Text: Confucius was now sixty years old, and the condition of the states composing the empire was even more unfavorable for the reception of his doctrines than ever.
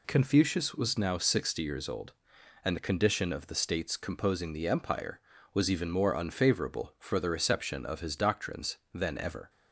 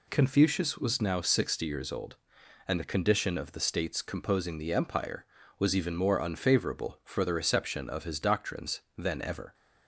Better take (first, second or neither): neither